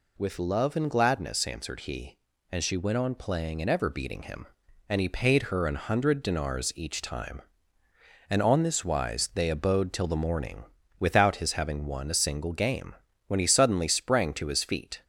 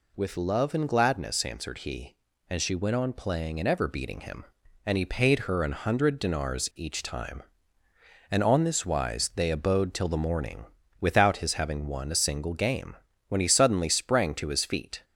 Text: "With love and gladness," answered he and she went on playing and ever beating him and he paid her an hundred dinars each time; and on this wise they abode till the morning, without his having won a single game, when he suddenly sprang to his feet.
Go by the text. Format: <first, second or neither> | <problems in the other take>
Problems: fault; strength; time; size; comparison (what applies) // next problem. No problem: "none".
neither | none